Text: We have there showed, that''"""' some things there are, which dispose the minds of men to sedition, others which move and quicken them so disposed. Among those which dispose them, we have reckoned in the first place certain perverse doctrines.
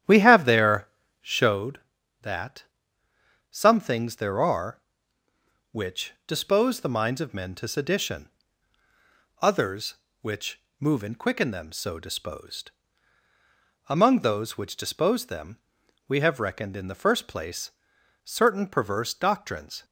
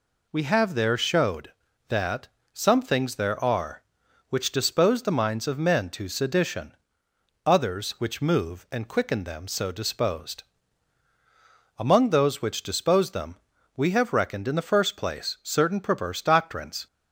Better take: second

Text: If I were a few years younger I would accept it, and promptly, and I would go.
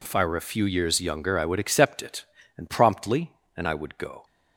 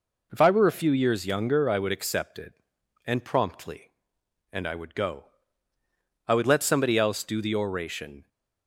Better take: first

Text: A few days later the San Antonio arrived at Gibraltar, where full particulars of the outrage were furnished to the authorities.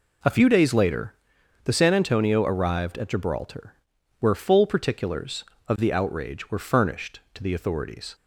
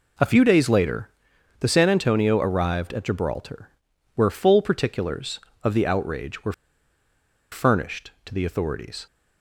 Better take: first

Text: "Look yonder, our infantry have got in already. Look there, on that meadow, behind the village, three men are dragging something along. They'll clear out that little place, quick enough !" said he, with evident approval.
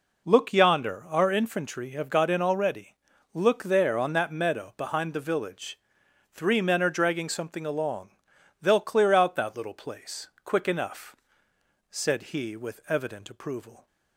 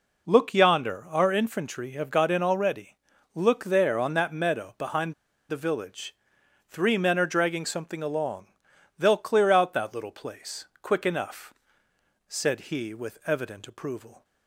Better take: first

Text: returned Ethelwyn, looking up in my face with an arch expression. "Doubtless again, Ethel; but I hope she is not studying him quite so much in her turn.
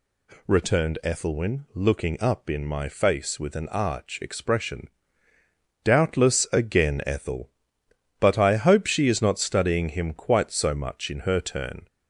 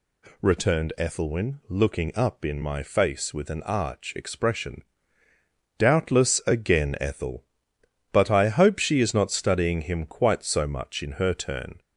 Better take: neither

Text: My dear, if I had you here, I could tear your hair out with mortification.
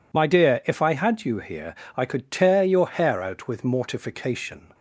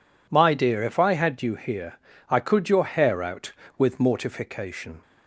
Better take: first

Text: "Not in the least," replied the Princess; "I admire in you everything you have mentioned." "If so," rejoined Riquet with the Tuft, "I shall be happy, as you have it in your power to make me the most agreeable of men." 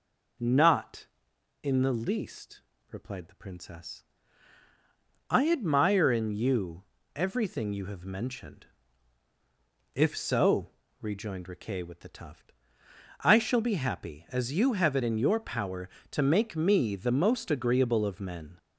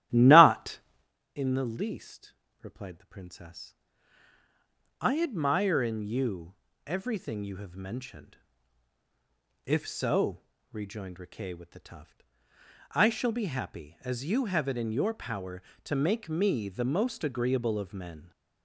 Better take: first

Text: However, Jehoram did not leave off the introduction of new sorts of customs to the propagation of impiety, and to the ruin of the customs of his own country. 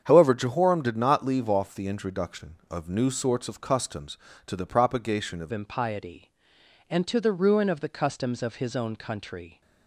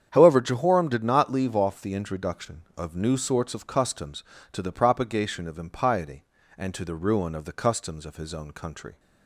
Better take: second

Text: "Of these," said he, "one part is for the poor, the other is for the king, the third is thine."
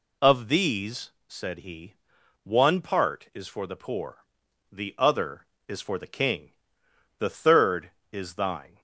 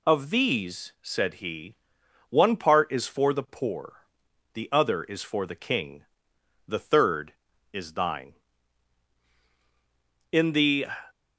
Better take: first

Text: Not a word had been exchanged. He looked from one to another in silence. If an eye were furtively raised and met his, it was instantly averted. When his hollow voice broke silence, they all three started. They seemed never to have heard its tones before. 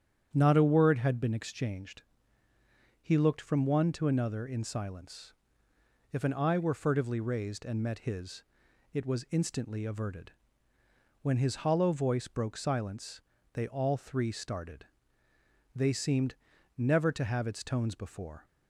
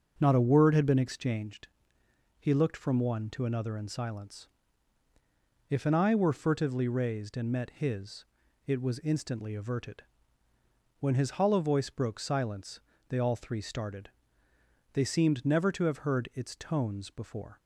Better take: second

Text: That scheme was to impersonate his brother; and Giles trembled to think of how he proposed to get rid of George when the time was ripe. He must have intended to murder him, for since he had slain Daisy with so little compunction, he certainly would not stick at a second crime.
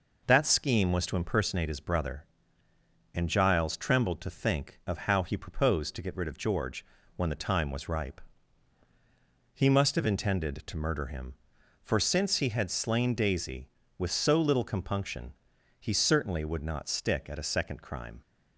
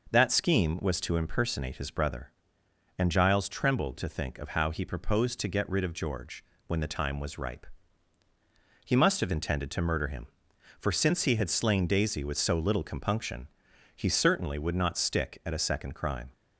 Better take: neither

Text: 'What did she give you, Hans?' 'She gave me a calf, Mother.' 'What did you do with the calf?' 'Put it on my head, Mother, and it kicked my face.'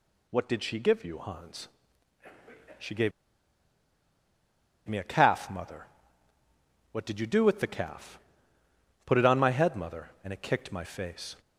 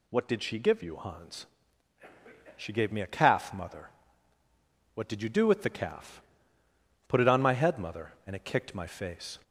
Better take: second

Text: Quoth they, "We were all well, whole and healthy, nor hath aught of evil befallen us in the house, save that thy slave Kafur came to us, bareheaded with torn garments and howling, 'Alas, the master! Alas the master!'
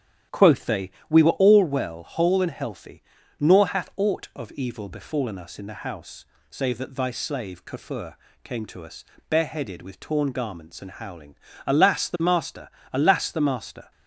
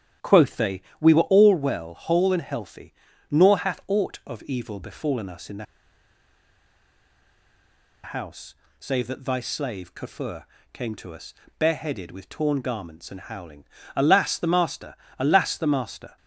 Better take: first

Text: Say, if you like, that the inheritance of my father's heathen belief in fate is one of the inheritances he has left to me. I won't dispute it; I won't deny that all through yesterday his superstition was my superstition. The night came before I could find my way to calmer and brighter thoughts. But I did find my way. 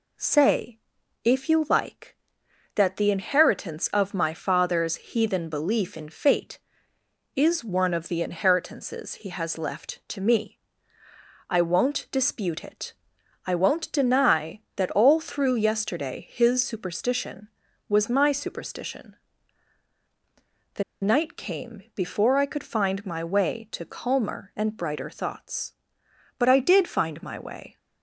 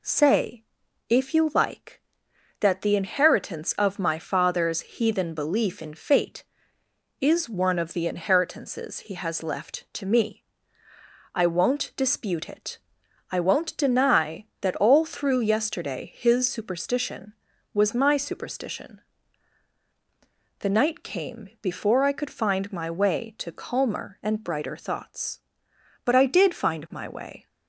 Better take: second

